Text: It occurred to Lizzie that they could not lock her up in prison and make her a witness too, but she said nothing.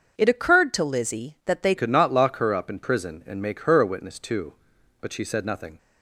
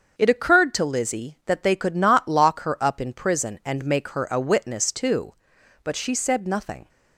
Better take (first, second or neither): second